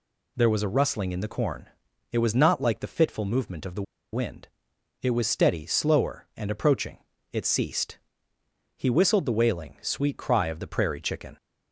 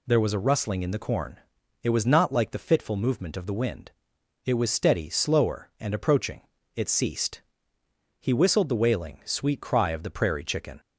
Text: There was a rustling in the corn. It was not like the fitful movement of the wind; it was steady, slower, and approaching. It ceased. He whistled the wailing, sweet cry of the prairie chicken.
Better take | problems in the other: second | pauses between "the" and "wind"; slight; at 3.8 s; 0.30 s long

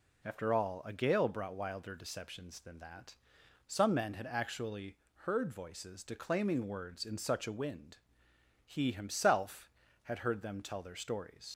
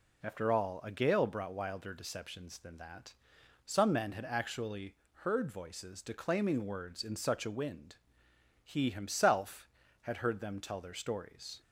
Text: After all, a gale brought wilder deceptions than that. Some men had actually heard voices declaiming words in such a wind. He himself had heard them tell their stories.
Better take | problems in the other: second | pauses between "actually" and "heard"; slight; at 4.9 s; 0.26 s long; slight in the second // leaves "stories" unfinished; at 11.4 s; 80 ms

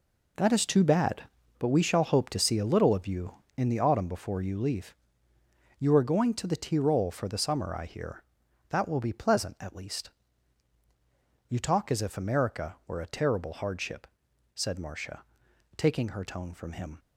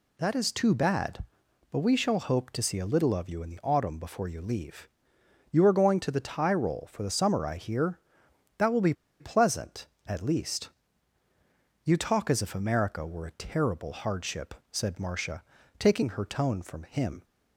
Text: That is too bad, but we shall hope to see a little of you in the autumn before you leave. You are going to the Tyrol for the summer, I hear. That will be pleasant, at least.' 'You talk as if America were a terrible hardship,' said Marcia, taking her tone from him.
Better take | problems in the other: first | pauses between "be" and "pleasant"; slight; at 8.9 s; 0.26 s long

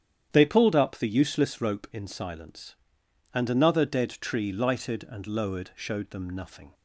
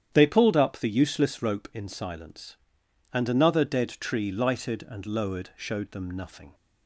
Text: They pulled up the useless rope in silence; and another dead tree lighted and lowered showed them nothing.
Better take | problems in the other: neither | starts louder than the rest; strong; the same in both

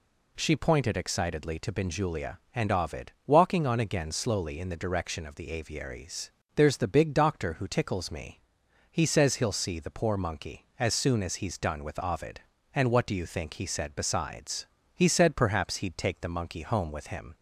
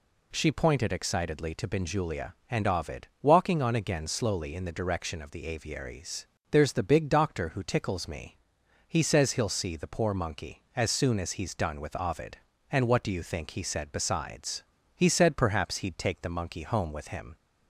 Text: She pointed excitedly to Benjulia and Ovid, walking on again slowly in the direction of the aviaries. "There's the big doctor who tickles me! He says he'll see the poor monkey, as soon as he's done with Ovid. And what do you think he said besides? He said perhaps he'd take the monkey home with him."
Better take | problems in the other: neither | none

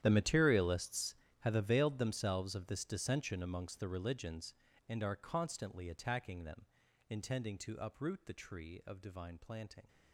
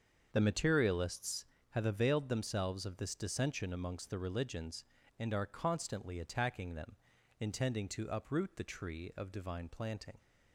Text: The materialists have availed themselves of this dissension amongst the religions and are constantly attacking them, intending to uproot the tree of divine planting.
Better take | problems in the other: second | gets quieter; strong; throughout; 18 dB // starts louder than the rest; strong; until 1.0 s; 10.5 dB; also in the second

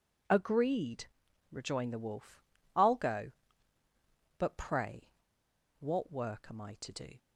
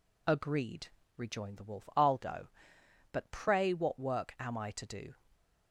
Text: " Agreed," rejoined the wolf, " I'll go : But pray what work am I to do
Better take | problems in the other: second | pauses between "pray" and "what"; noticeable; at 5.1 s; 0.69 s long

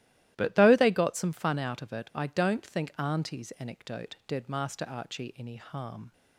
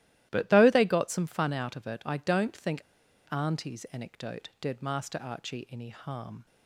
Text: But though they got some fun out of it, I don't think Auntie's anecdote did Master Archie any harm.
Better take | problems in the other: first | starts louder than the rest; strong; until 1.3 s; 14.5 dB; strong in the first // pauses between "think" and "Auntie's"; noticeable; at 2.8 s; 0.47 s long

